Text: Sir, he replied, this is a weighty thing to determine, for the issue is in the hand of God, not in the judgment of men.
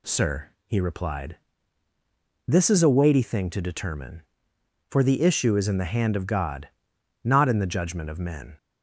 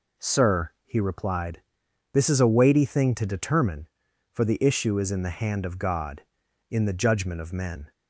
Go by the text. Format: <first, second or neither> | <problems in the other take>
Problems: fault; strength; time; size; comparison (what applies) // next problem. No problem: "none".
first | skips "not"; at 6.4 s